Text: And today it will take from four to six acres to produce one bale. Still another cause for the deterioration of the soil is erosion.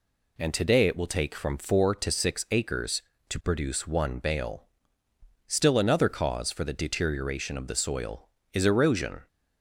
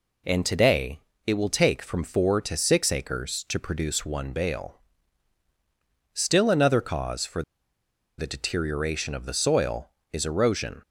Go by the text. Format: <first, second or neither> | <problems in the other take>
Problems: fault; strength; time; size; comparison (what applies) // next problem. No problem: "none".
first | pauses between "today" and "it"; slight; at 0.9 s; 0.26 s long // pauses between "for" and "the"; noticeable; at 7.4 s; 0.76 s long